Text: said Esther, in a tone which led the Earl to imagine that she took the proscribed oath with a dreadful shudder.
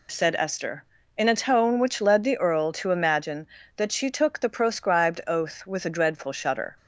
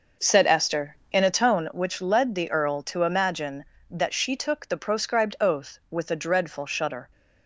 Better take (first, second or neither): first